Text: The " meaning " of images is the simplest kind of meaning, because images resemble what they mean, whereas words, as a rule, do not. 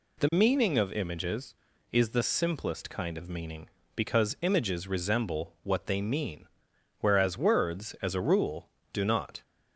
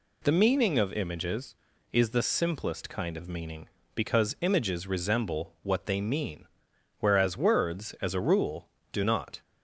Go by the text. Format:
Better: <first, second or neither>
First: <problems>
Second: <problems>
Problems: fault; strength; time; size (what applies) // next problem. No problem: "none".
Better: neither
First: none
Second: none